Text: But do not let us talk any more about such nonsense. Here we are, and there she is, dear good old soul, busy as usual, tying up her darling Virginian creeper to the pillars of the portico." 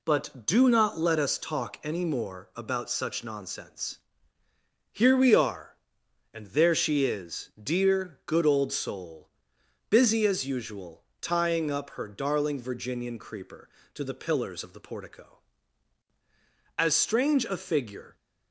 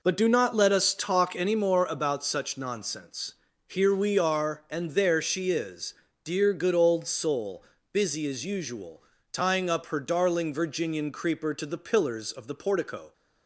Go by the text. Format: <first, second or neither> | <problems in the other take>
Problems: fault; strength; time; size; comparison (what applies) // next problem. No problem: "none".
second | goes on to say "As strange a figure"; from 16.7 s on; 1.3 s long